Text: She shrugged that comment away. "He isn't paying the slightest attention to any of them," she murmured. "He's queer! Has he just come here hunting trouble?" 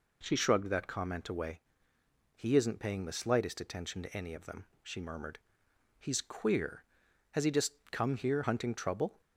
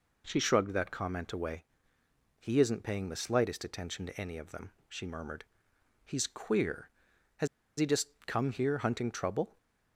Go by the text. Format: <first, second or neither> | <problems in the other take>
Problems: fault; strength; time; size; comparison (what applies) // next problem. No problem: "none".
first | pauses between "Has" and "he"; slight; at 7.4 s; 0.31 s long // pauses between "just" and "come"; slight; at 8.0 s; 0.18 s long; slight in the first